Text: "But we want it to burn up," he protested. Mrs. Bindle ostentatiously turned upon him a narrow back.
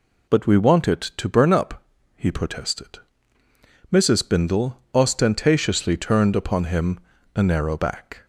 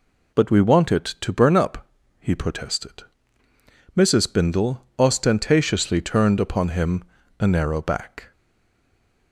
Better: first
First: pauses between "him" and "a"; slight; at 6.9 s; 0.34 s long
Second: pauses between "him" and "a"; slight; at 7.0 s; 0.34 s long // stays silent after the last word; from 8.3 s on; 1.0 s long

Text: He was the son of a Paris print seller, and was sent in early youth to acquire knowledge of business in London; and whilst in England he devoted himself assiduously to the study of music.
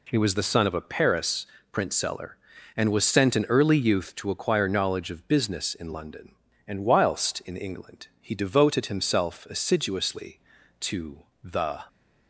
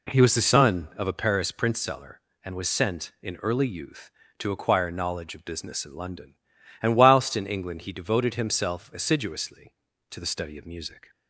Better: second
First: pauses between "Paris" and "print"; slight; at 1.4 s; 0.26 s long // pauses between "to" and "the"; slight; at 11.2 s; 0.20 s long // stops before "study of music"; at 11.8 s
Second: none

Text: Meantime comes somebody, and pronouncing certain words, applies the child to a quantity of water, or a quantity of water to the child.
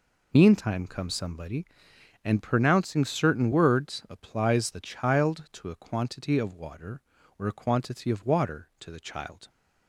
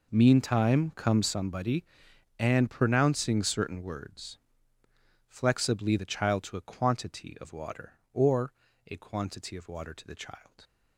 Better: first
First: none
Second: says "flexibly" for "applies"; at 5.2 s // pauses between "or" and "a"; slight; at 8.5 s; 0.34 s long

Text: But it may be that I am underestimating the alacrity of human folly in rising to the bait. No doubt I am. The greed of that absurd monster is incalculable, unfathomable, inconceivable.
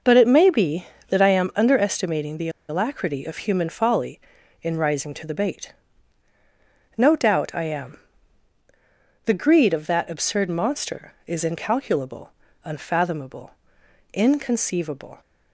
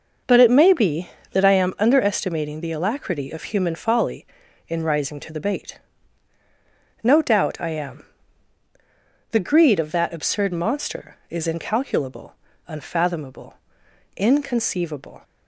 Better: second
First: pauses between "the" and "alacrity"; slight; at 2.4 s; 0.20 s long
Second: none

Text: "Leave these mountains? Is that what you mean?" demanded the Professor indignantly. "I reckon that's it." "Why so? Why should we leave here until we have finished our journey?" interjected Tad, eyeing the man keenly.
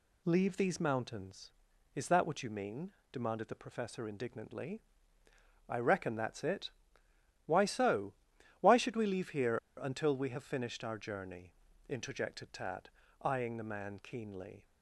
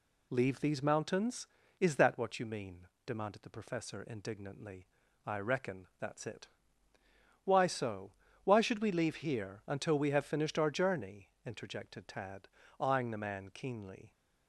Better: second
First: pauses between "here" and "until"; slight; at 9.5 s; 0.18 s long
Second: none

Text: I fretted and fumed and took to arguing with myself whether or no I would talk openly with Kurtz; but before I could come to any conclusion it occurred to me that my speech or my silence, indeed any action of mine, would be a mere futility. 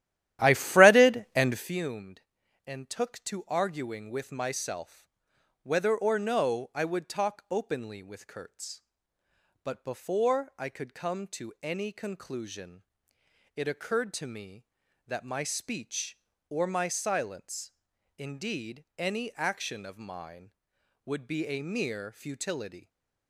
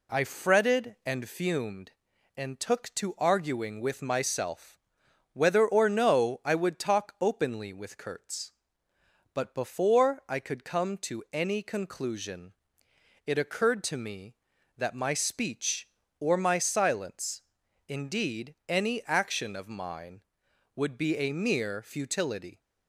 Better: second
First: starts louder than the rest; strong; until 1.8 s; 13 dB // pauses between "myself" and "whether"; noticeable; at 5.0 s; 0.58 s long // pauses between "conclusion" and "it"; noticeable; at 12.8 s; 0.70 s long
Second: pauses between "myself" and "whether"; noticeable; at 4.7 s; 0.58 s long // pauses between "conclusion" and "it"; noticeable; at 12.5 s; 0.70 s long

